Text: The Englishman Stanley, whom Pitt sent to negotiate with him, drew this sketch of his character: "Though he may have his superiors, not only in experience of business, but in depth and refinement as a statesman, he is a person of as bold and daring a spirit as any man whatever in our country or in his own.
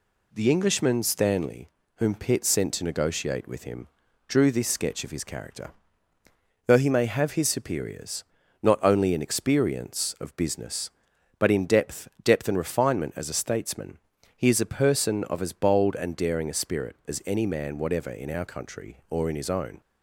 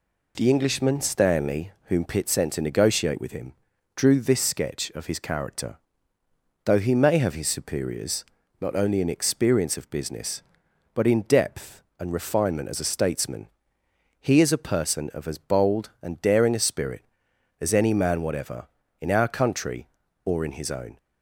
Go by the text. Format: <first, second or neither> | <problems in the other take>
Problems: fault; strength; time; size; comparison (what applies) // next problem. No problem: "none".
second | says "depth" twice; at 12.2 s